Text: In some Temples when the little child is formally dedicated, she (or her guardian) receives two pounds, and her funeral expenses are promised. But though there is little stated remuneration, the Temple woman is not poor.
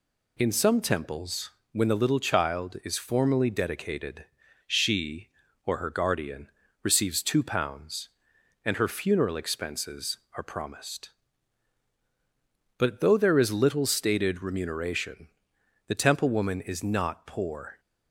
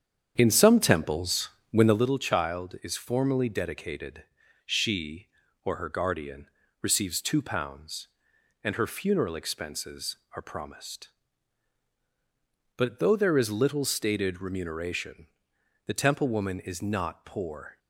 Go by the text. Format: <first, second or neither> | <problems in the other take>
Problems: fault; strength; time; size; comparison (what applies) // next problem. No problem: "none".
first | starts louder than the rest; strong; until 2.1 s; 8 dB // pauses between "Temples" and "when"; slight; at 1.4 s; 0.22 s long; slight in the first